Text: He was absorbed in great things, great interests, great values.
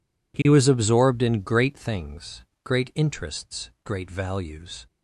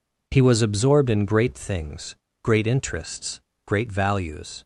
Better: neither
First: none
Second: none

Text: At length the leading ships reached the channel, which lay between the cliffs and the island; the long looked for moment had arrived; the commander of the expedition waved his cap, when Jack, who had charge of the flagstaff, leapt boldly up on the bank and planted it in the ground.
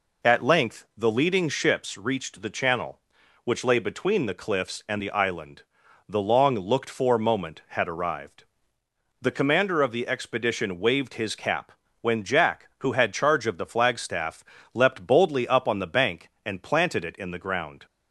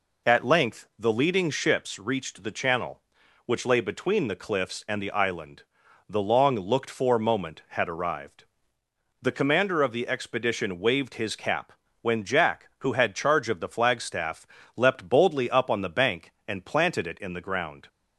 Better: neither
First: none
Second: none

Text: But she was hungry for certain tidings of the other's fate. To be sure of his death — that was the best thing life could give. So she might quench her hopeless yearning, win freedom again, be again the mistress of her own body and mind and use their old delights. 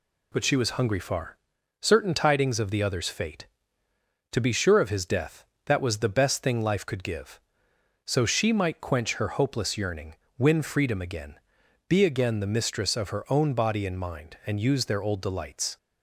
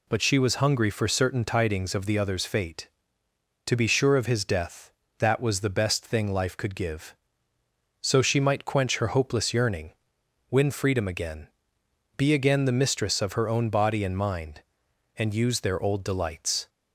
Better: second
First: says "far" for "for"; at 0.9 s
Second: none

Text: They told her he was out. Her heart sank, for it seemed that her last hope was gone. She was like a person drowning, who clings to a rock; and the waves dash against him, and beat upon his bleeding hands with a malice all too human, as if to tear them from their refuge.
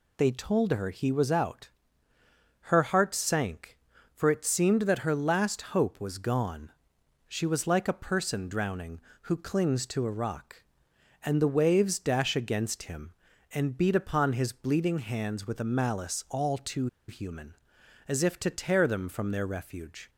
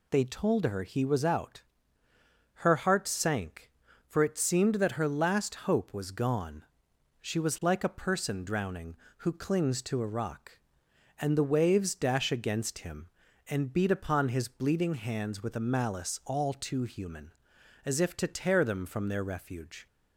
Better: second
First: pauses between "too" and "human"; slight; at 16.8 s; 0.21 s long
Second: none

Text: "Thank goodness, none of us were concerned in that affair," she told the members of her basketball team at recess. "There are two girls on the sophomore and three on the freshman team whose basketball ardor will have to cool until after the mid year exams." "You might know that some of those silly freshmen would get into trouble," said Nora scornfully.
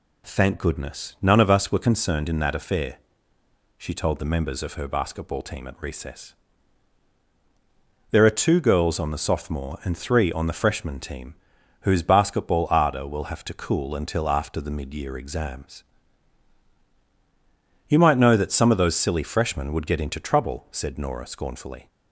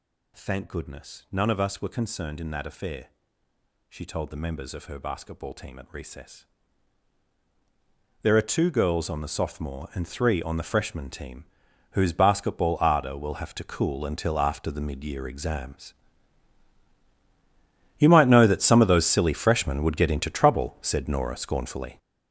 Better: first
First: pauses between "team" and "whose"; noticeable; at 11.3 s; 0.46 s long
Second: gets louder; strong; throughout; 10.5 dB // pauses between "team" and "whose"; noticeable; at 11.4 s; 0.46 s long

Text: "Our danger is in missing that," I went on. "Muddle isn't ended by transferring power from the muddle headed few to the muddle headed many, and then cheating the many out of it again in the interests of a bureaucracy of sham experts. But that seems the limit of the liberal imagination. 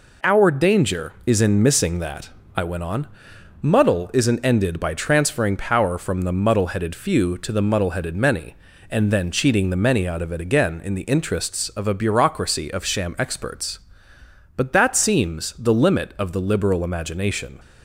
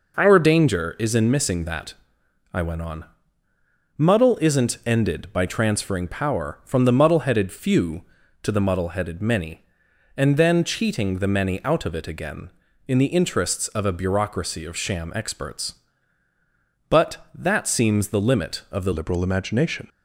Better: first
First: none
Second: changes voice at "liberal"; from 18.9 s on; 0.9 s long

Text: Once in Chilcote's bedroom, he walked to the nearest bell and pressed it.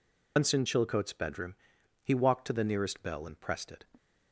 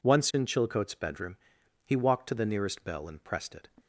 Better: second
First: loses the start of "Once"; at 0.3 s; 115 ms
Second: none

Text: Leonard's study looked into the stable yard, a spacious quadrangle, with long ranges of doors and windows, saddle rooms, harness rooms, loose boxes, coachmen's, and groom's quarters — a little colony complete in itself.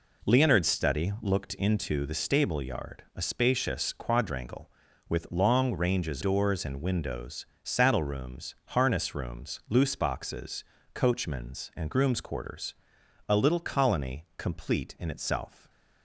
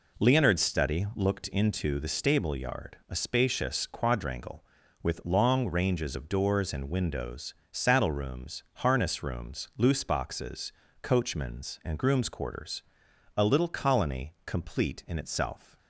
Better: second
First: skips "of"; at 6.2 s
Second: none

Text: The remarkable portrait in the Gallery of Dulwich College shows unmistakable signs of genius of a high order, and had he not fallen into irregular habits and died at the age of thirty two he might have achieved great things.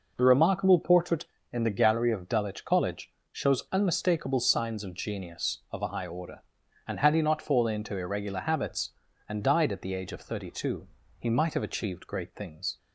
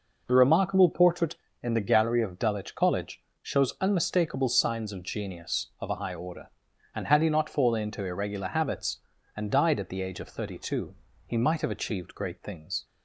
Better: neither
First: pauses between "College" and "shows"; slight; at 3.1 s; 0.20 s long // pauses between "two" and "he"; slight; at 10.8 s; 0.32 s long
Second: pauses between "College" and "shows"; slight; at 3.2 s; 0.20 s long // pauses between "two" and "he"; slight; at 10.9 s; 0.32 s long

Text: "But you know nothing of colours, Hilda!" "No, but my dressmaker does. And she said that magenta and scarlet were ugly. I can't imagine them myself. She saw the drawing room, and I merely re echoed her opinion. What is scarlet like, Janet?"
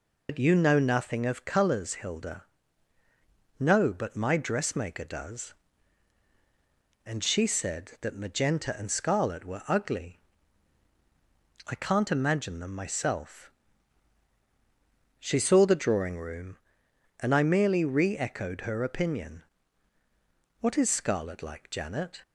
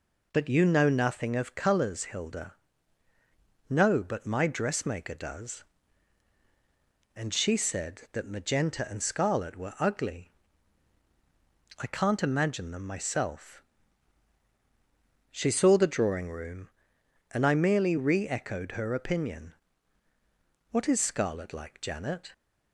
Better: second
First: loses the start of "But"; at 0.2 s; 80 ms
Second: none

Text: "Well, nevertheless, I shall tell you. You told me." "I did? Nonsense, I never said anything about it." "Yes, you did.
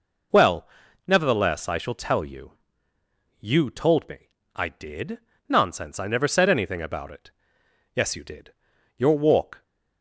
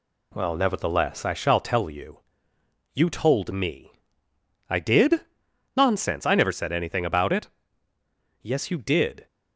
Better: second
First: goes on to say "Your walk"; noticeable; from 8.9 s on; 0.66 s long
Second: none

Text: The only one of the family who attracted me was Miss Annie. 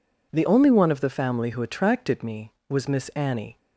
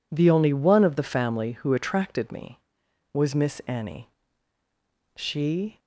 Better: first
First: none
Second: goes on to say "She"; noticeable; from 5.1 s on; 0.62 s long

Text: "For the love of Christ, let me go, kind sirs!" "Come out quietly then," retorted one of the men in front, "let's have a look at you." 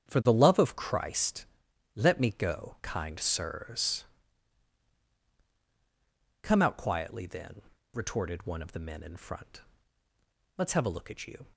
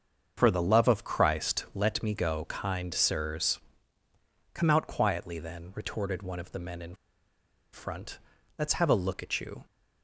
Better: first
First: starts louder than the rest; strong; until 1.1 s; 8.5 dB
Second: starts louder than the rest; until 1.3 s; 7 dB // pauses between "in" and "front"; noticeable; at 6.9 s; 0.78 s long

